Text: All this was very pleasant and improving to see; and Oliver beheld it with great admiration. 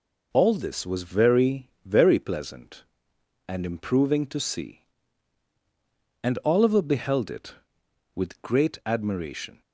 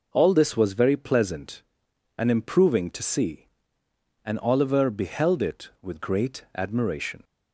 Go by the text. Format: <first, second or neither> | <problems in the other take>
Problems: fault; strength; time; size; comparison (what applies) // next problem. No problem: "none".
second | says "very" twice; at 1.8 s